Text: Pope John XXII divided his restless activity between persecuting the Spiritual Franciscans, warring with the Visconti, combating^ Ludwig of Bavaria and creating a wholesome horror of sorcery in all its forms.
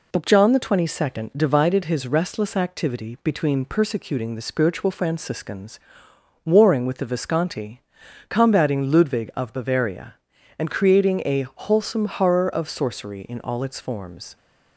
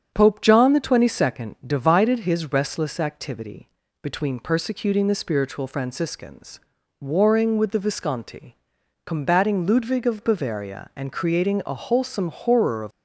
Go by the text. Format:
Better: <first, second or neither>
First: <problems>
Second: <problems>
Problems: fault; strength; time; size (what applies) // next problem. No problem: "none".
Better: first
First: none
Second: starts louder than the rest; strong; until 1.1 s; 7.5 dB // pauses between "activity" and "between"; slight; at 3.7 s; 0.32 s long // stops before "sorcery in all its forms"; at 12.9 s